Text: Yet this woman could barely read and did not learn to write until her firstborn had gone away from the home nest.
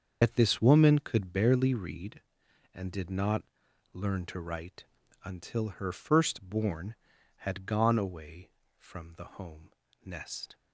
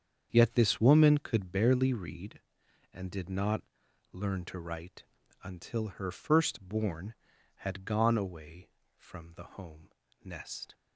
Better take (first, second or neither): second